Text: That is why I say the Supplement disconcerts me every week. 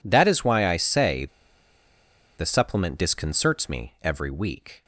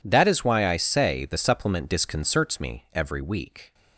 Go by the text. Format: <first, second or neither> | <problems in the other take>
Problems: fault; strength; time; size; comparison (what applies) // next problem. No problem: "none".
second | pauses between "say" and "the"; at 1.2 s; 1.1 s long